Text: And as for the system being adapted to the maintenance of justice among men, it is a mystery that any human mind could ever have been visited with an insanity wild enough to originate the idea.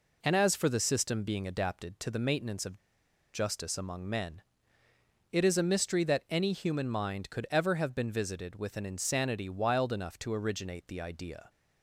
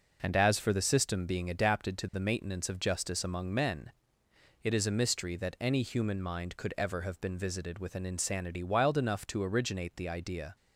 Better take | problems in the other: second | pauses between "of" and "justice"; noticeable; at 2.7 s; 0.57 s long

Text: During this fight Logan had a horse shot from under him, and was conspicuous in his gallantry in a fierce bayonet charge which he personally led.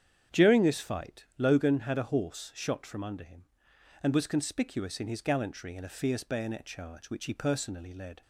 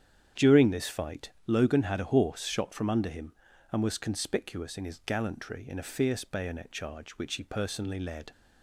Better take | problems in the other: neither | starts louder than the rest; strong; the same in both

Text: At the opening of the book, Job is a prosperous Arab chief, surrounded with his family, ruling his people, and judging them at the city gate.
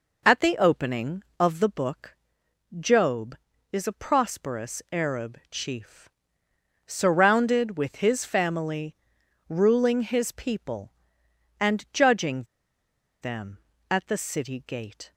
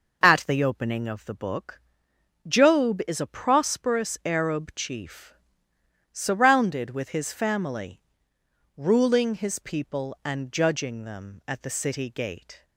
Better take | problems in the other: second | pauses between "judging" and "them"; noticeable; at 12.4 s; 0.77 s long

